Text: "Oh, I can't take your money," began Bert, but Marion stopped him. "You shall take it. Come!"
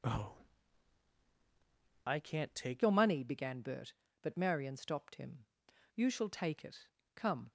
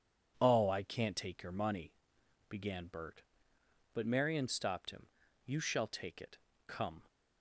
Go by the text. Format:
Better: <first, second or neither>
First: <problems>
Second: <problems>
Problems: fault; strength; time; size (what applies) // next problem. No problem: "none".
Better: second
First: changes voice at "your"; from 2.8 s on; 4.7 s long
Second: none